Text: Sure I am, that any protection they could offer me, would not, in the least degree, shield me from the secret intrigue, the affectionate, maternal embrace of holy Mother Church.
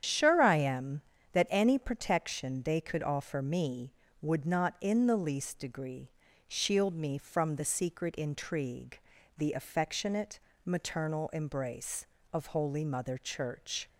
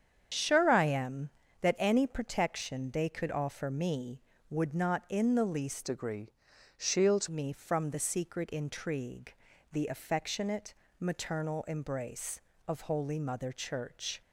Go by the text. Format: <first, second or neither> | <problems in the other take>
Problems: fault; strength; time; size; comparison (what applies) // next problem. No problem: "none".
first | starts louder than the rest; strong; until 1.6 s; 8 dB; strong in the first // changes voice from "degree" to "shield"; from 5.8 to 7.2 s; 1.4 s long